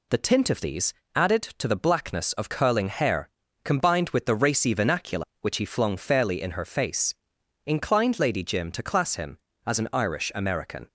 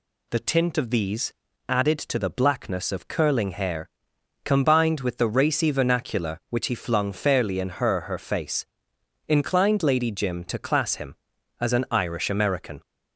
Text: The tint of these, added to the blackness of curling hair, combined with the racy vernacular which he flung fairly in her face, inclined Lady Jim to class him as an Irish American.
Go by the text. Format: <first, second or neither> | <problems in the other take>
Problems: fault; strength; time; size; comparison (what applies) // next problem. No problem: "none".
first | says "her" twice; at 8.0 s